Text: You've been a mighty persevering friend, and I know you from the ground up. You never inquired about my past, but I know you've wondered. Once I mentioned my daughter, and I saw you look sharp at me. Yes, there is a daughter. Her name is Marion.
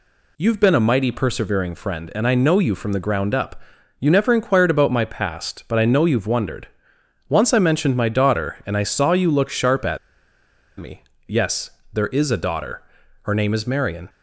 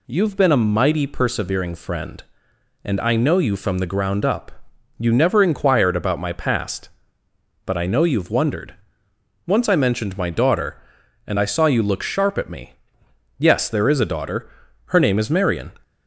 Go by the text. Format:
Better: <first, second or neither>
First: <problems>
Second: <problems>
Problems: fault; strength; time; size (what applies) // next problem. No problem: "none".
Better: second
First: pauses between "at" and "me"; noticeable; at 9.9 s; 0.81 s long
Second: none